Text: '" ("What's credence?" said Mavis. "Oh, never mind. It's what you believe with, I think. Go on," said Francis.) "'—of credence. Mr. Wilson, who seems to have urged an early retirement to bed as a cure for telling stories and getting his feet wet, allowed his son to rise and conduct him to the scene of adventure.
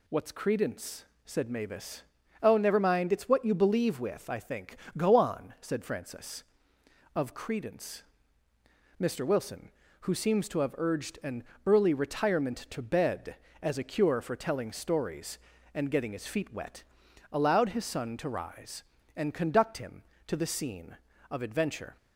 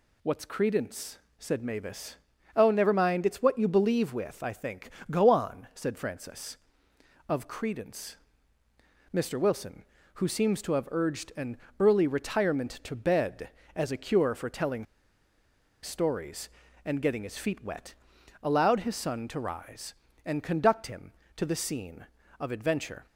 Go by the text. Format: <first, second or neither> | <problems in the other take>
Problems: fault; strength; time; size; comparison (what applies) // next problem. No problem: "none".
first | pauses between "an" and "early"; slight; at 11.5 s; 0.22 s long; slight in the first // pauses between "telling" and "stories"; noticeable; at 14.8 s; 0.97 s long